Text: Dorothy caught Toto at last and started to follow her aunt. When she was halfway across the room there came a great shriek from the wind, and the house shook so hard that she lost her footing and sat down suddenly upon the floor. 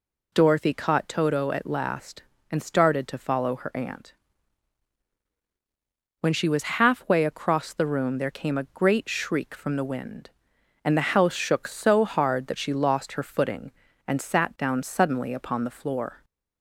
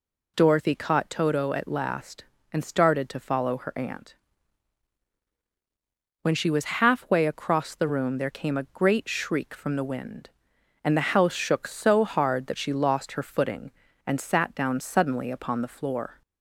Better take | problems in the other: neither | none

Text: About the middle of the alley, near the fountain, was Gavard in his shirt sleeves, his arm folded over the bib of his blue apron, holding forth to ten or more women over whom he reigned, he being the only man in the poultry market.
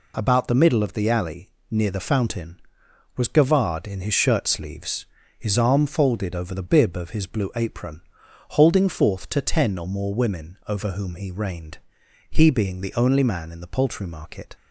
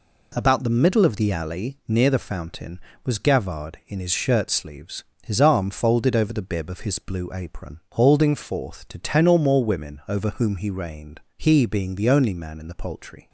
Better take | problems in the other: first | stops before "market"; at 13.2 s

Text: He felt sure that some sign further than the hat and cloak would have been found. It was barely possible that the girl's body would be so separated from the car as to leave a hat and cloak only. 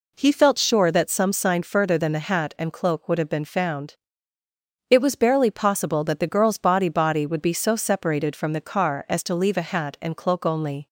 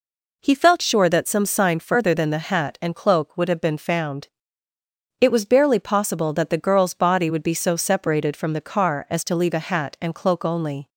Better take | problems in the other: second | says "body" twice; at 6.8 s

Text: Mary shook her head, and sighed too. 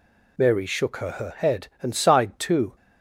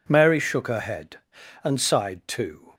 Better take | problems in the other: second | says "her" twice; at 1.1 s

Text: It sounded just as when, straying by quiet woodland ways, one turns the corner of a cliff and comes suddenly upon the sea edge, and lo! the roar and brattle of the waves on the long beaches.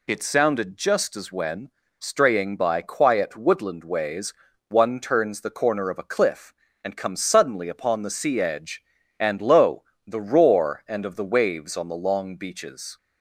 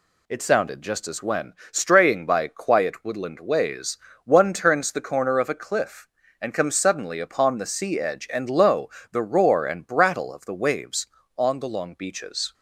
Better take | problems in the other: second | skips "brattle"; at 11.0 s

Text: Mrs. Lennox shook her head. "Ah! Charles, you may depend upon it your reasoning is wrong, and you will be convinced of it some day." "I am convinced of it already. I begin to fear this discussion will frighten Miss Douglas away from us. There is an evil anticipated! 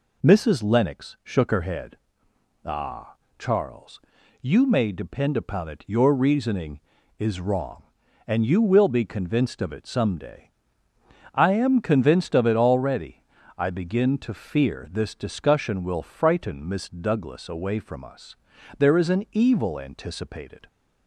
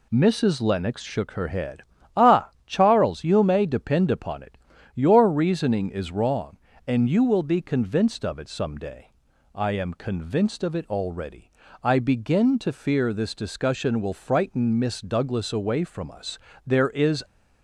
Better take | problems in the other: first | pauses between "it" and "your"; at 4.5 s; 0.42 s long // stops before "an evil anticipated"; at 17.2 s

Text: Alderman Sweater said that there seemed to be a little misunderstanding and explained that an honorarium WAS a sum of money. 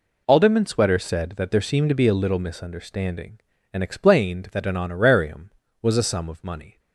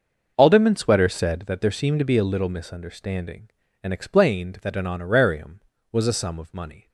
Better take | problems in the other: first | starts louder than the rest; noticeable; until 1.6 s; 6 dB

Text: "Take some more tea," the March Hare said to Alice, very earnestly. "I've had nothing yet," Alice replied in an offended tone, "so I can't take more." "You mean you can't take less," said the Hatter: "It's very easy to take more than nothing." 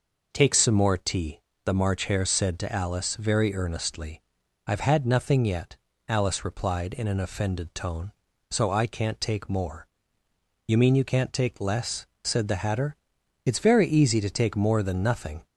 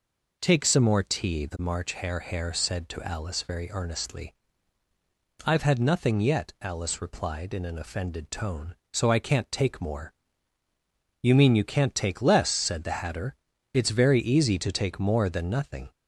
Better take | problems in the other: first | says "Hare" twice; at 2.2 s

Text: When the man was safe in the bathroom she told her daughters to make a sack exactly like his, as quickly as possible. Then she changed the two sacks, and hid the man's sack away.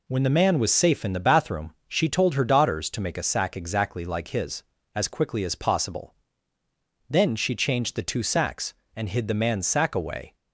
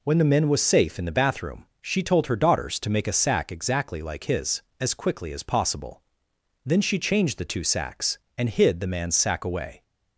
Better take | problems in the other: first | says "men" for "man"; at 0.2 s

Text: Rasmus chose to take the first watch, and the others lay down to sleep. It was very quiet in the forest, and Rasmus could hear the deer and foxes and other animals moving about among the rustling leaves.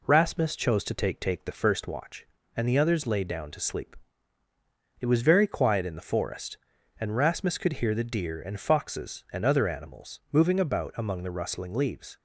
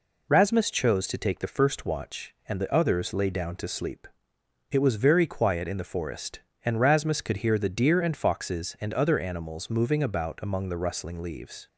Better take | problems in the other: second | says "take" twice; at 1.2 s

